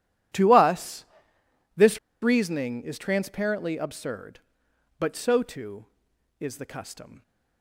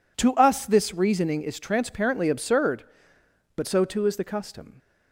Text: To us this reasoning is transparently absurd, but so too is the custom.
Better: second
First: pauses between "us" and "this"; noticeable; at 1.0 s; 0.70 s long // pauses between "this" and "reasoning"; slight; at 1.9 s; 0.23 s long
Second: none

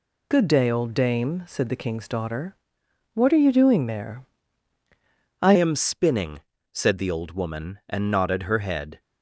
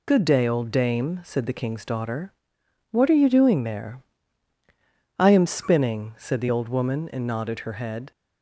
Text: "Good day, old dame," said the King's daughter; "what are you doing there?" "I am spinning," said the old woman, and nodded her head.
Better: second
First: changes voice at "am"; from 5.5 s on; 3.4 s long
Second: none

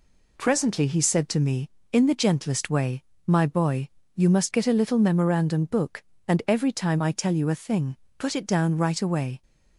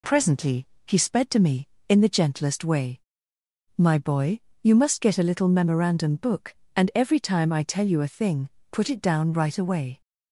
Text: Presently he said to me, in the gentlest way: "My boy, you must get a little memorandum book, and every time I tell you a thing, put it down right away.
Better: first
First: none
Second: pauses between "Presently" and "he"; slight; at 0.6 s; 0.18 s long // says "sped" for "said"; at 0.9 s

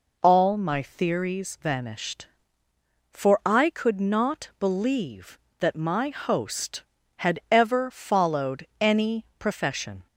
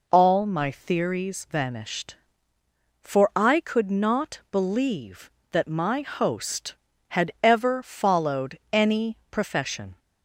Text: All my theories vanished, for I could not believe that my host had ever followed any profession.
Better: neither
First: pauses between "followed" and "any"; slight; at 8.6 s; 0.16 s long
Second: pauses between "followed" and "any"; slight; at 8.5 s; 0.16 s long

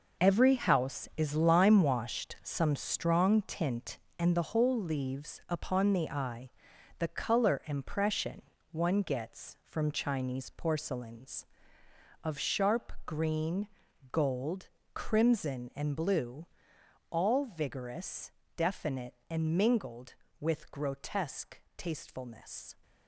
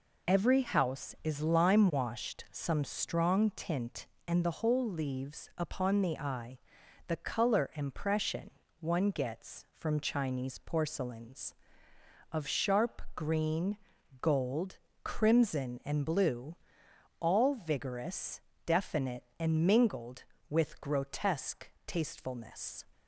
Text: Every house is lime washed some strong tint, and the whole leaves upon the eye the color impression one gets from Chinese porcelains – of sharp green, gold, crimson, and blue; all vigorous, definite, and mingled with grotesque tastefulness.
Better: second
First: gets quieter; strong; throughout; 9.5 dB // pauses between "eye" and "the"; noticeable; at 6.5 s; 0.50 s long // pauses between "impression" and "one"; slight; at 8.4 s; 0.28 s long // pauses between "sharp" and "green"; slight; at 12.8 s; 0.18 s long // pauses between "grotesque" and "tastefulness"; slight; at 21.5 s; 0.16 s long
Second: pauses between "eye" and "the"; noticeable; at 6.5 s; 0.50 s long // pauses between "impression" and "one"; slight; at 8.5 s; 0.28 s long // pauses between "sharp" and "green"; slight; at 13.0 s; 0.16 s long // pauses between "grotesque" and "tastefulness"; slight; at 21.6 s; 0.16 s long

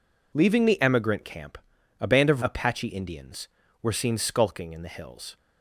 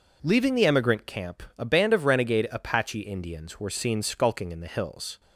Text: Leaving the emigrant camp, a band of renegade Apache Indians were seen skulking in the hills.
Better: second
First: skips "renegade"; at 2.4 s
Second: none

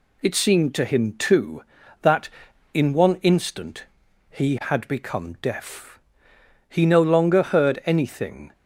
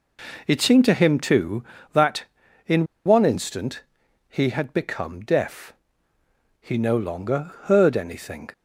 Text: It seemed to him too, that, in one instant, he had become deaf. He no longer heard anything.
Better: first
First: none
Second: pauses between "in" and "one"; slight; at 2.8 s; 0.21 s long

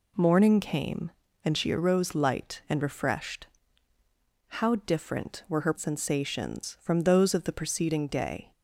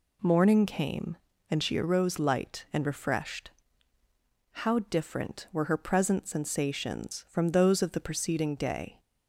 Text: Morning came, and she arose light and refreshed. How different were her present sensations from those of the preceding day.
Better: second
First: skips "present"; at 5.7 s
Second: none

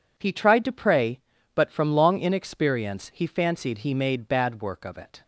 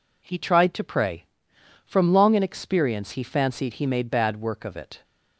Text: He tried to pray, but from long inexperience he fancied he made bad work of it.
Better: first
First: none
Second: skips "but"; at 1.5 s

